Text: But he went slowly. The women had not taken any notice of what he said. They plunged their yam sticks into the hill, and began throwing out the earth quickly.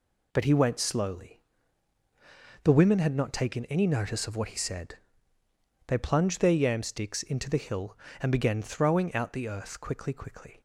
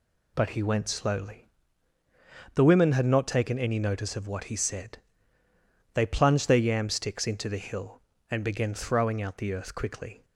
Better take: second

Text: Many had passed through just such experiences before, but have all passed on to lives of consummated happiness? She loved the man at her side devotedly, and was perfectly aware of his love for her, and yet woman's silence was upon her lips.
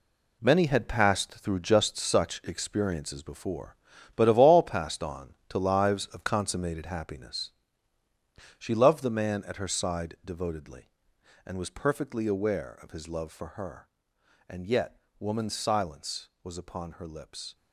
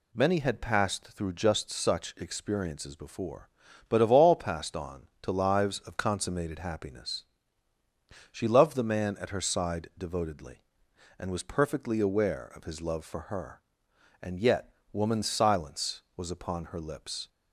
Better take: second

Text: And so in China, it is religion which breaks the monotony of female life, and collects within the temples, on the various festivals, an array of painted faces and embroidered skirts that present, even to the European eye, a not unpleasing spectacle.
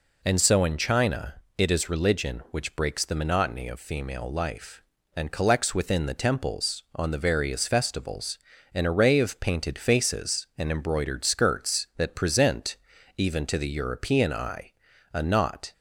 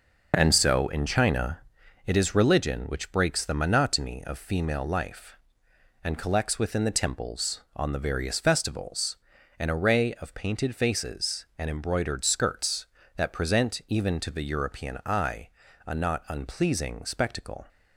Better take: second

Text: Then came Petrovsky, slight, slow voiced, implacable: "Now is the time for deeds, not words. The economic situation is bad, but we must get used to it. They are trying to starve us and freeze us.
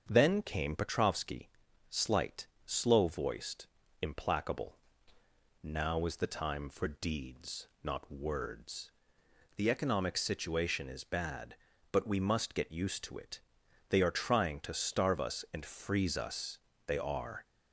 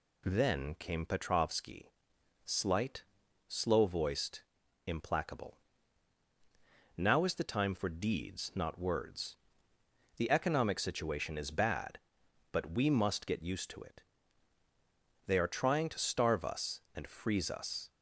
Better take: second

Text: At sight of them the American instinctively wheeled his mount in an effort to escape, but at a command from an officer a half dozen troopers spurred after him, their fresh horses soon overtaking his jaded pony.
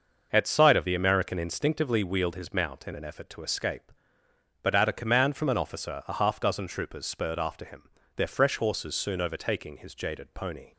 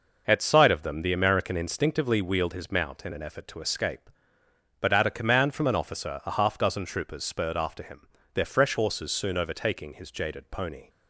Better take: second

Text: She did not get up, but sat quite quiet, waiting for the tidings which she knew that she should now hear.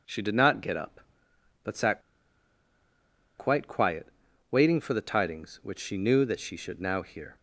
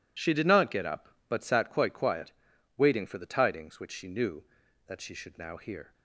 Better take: second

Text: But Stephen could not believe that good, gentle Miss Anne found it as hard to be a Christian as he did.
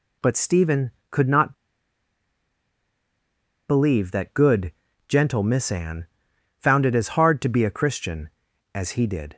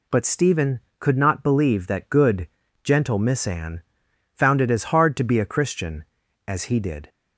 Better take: second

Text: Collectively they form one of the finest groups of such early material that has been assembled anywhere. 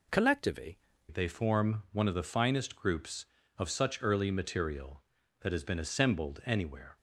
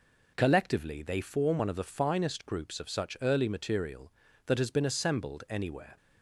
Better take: second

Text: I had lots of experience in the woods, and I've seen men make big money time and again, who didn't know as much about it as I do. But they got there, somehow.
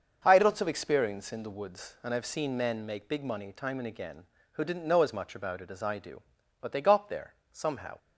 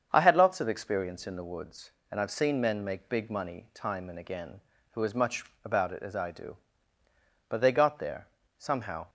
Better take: first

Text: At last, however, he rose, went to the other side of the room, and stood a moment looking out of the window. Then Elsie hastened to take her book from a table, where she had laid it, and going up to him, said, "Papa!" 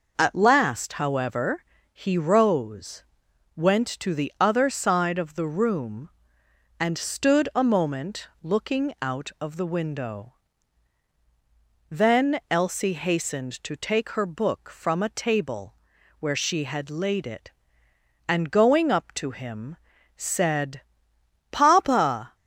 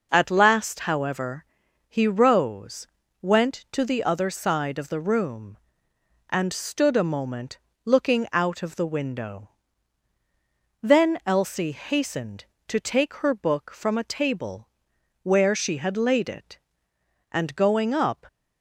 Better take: first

